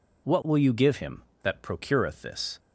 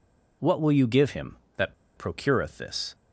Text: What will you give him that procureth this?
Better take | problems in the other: first | pauses between "that" and "procureth"; slight; at 1.7 s; 0.23 s long

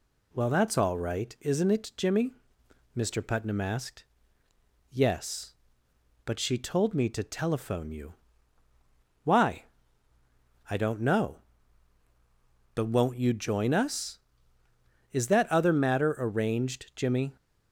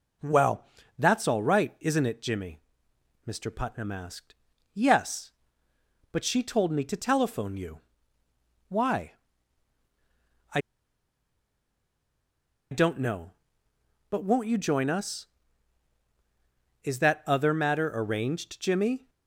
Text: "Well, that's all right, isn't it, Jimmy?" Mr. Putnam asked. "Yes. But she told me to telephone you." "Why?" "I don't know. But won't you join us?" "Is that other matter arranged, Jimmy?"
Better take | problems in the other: first | pauses between "I" and "don't"; strong; at 10.5 s; 2.1 s long

